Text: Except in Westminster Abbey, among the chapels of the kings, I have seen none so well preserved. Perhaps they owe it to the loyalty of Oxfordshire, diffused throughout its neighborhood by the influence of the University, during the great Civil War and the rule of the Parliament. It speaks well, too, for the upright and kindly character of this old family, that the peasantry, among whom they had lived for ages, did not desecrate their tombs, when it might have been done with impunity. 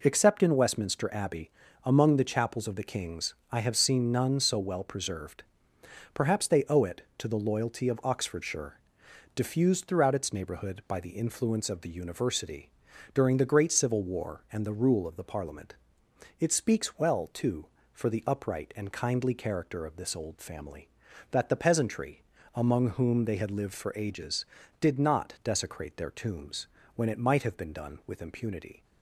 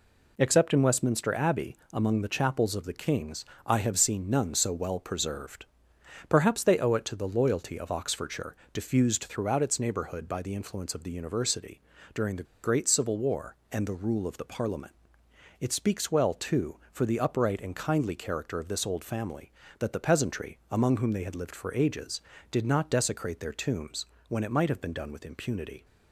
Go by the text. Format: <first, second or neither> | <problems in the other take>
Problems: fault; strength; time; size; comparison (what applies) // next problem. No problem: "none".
first | pauses between "the" and "great"; slight; at 12.4 s; 0.20 s long